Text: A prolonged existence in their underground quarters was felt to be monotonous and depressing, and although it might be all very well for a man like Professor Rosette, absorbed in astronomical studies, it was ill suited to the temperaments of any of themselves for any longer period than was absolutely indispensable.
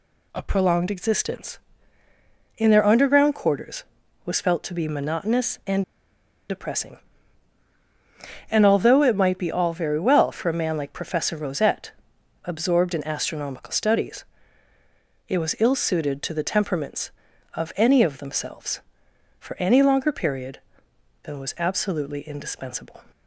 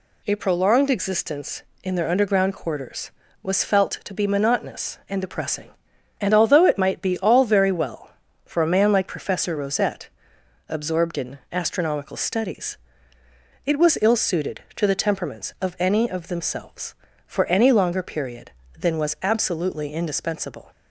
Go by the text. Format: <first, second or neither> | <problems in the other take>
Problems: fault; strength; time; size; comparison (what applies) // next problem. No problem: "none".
second | pauses between "and" and "depressing"; noticeable; at 5.8 s; 0.67 s long